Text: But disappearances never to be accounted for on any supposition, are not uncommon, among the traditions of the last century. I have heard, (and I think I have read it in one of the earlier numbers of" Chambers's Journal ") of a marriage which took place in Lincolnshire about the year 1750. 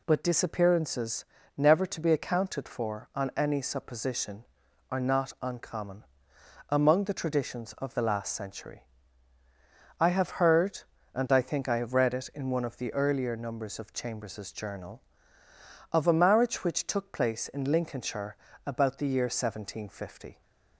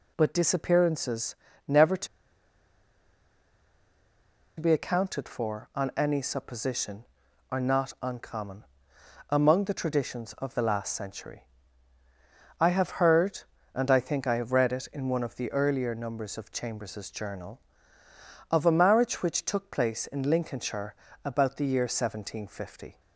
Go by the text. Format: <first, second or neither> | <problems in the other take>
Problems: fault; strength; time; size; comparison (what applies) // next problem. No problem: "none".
first | pauses between "disappearances" and "never"; slight; at 1.3 s; 0.30 s long; slight in the first // pauses between "to" and "be"; strong; at 2.0 s; 2.5 s long // pauses between "Lincolnshire" and "about"; slight; at 20.9 s; 0.30 s long; slight in the first